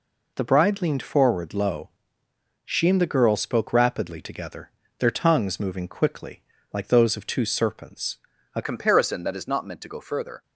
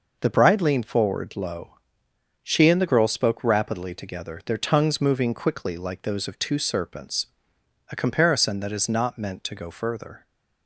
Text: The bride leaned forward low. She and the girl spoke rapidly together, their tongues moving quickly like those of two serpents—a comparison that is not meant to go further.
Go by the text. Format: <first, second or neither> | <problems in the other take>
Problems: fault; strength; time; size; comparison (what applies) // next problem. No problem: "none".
second | pauses between "quickly" and "like"; slight; at 6.4 s; 0.30 s long // changes voice at "comparison"; from 8.6 s on; 1.8 s long